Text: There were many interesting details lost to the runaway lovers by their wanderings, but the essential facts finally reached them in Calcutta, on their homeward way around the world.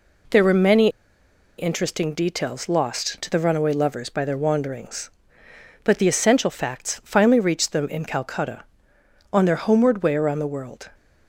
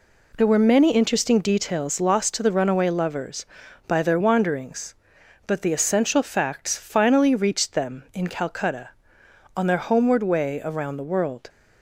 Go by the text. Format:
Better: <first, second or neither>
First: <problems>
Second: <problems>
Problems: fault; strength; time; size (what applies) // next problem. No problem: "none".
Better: second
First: pauses between "many" and "interesting"; noticeable; at 0.8 s; 0.70 s long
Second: none